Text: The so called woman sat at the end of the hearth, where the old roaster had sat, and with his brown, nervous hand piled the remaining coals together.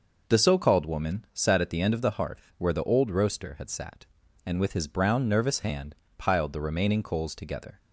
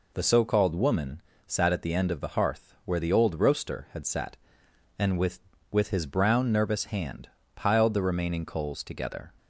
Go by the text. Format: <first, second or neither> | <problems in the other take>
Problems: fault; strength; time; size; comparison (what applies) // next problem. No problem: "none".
first | pauses between "woman" and "sat"; slight; at 1.2 s; 0.26 s long // says "with" twice; at 5.7 s // pauses between "hand" and "piled"; slight; at 7.2 s; 0.26 s long; slight in the first